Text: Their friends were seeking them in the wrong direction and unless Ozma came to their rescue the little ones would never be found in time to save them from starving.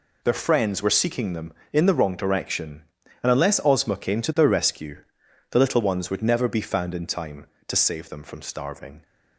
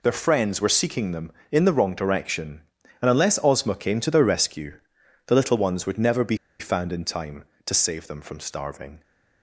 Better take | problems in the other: first | pauses between "rescue" and "the"; noticeable; at 4.7 s; 0.48 s long; noticeable in the first // pauses between "be" and "found"; slight; at 6.3 s; 0.23 s long

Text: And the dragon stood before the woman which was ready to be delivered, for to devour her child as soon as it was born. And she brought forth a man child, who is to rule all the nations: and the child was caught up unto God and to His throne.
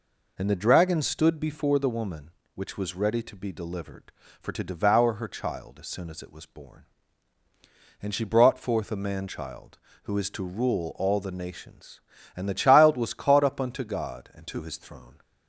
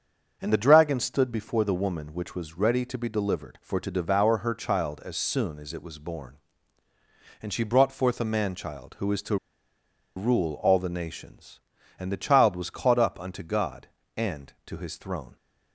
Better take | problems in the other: first | starts louder than the rest; until 1.4 s; 7 dB // pauses between "to" and "rule"; noticeable; at 9.3 s; 0.80 s long

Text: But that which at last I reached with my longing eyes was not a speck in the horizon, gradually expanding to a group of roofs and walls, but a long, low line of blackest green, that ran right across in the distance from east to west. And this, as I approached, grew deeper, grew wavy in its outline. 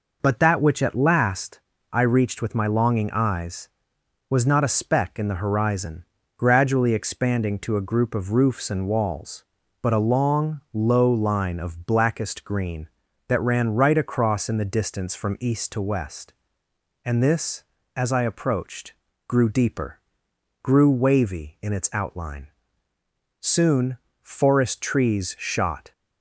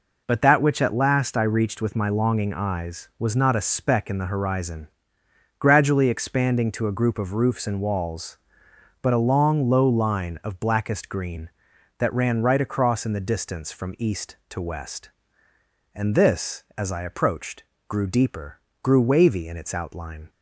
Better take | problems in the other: second | pauses between "last" and "I"; slight; at 1.5 s; 0.32 s long // goes on to say "Soon forest trees shot"; strong; from 23.3 s on; 2.5 s long

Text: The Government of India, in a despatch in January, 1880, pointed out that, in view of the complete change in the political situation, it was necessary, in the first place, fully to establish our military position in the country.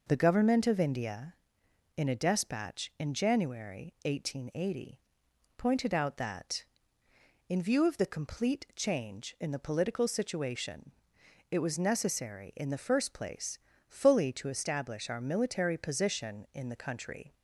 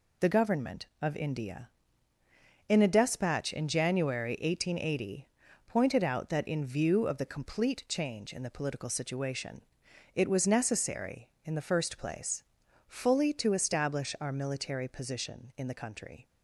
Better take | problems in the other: neither | none

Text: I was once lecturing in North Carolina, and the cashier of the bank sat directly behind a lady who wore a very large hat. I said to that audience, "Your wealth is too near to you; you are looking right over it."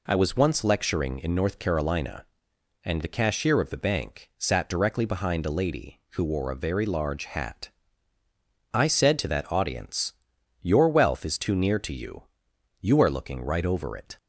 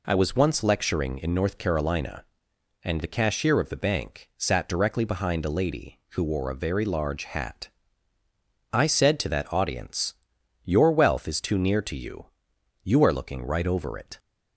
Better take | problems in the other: neither | none

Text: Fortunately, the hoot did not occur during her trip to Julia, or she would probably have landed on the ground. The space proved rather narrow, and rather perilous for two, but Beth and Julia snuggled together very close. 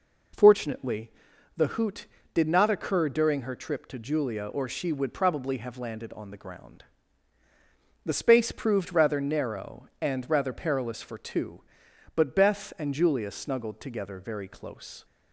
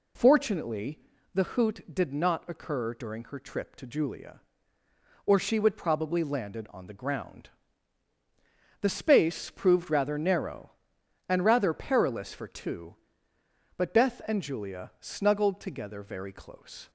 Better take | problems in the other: first | skips "have"; at 6.2 s

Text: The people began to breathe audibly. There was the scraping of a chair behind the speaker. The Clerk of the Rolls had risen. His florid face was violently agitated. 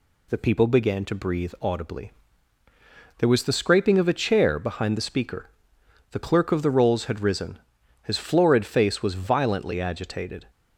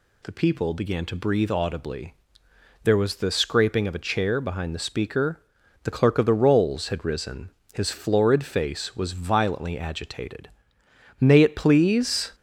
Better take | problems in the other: first | goes on to say "May it please"; noticeable; from 11.1 s on; 1.1 s long

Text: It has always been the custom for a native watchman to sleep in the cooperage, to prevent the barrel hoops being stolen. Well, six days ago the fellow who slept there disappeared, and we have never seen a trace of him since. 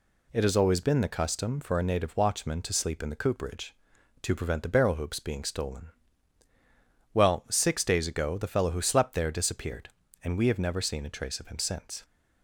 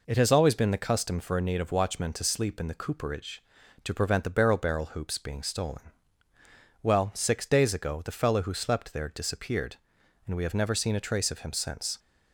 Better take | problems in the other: first | says "barrel" twice; at 4.5 s

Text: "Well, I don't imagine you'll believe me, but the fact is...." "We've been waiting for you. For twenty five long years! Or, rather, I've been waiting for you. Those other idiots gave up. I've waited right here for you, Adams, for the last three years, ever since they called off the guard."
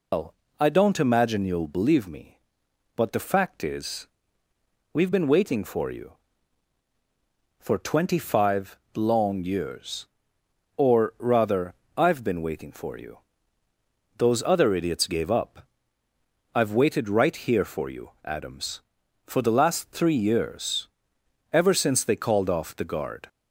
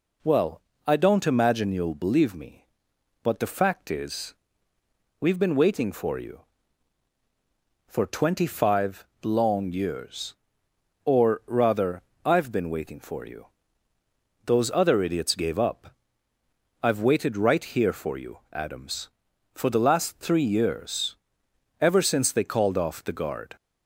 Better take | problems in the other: second | loses the start of "Well"; at 0.1 s; 175 ms // pauses between "five" and "long"; slight; at 8.7 s; 0.18 s long; slight in the second

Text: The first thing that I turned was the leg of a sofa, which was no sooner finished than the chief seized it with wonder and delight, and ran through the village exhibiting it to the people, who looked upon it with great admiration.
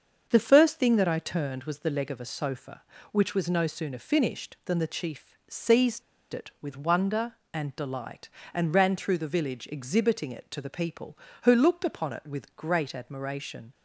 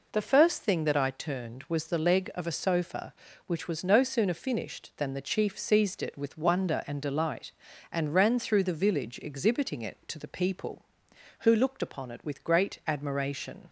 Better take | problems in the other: second | starts louder than the rest; until 1.3 s; 6.5 dB // pauses between "seized" and "it"; slight; at 6.0 s; 0.31 s long

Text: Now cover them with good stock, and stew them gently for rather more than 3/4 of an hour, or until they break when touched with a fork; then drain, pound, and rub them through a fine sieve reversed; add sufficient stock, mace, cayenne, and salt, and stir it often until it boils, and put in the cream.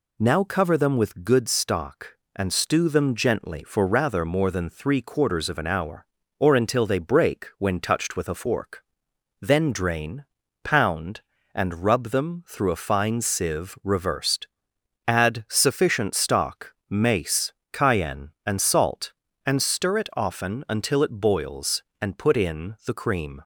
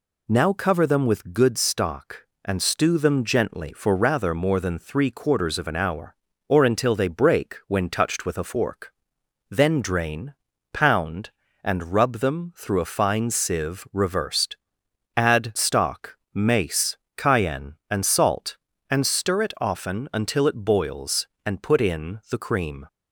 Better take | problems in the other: first | skips "sufficient"; at 15.5 s

